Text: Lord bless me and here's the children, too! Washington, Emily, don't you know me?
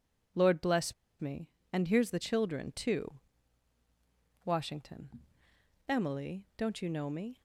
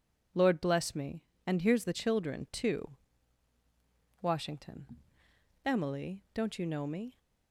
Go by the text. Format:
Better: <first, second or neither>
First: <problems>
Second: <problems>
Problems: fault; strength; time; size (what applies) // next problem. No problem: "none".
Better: second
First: pauses between "bless" and "me"; slight; at 0.9 s; 0.27 s long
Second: none